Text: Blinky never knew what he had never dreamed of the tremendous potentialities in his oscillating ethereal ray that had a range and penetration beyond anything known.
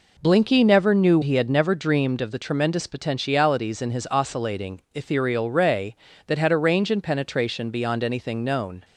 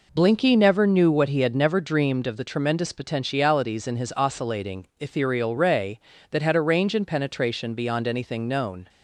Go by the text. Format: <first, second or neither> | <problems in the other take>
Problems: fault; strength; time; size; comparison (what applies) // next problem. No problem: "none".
second | skips "what"; at 1.2 s